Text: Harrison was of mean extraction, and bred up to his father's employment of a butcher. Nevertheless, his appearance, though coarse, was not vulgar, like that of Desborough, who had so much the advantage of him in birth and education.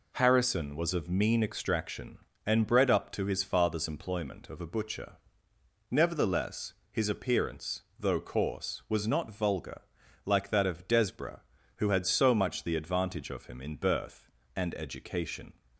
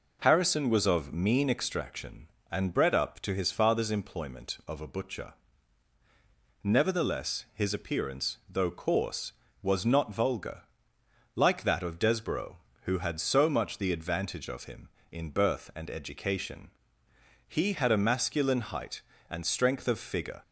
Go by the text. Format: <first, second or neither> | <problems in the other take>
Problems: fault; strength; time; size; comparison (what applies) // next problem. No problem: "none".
first | goes on to say "He had a masculine height and strength of figure"; strong; from 17.4 s on; 2.9 s long